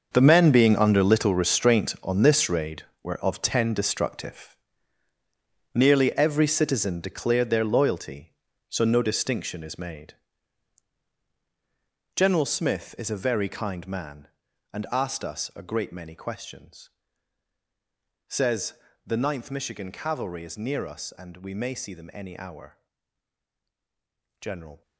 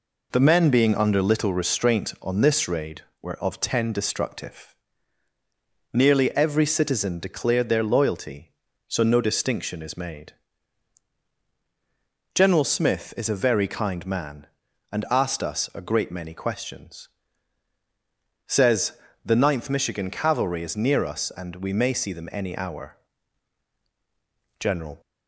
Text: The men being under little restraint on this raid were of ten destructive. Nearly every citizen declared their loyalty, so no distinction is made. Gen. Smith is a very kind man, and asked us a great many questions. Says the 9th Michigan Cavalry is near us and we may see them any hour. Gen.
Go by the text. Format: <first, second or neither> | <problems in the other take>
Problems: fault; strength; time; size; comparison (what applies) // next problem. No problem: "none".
second | gets quieter; strong; throughout; 13.5 dB // pauses between "Says" and "the"; slight; at 18.7 s; 0.32 s long; slight in the second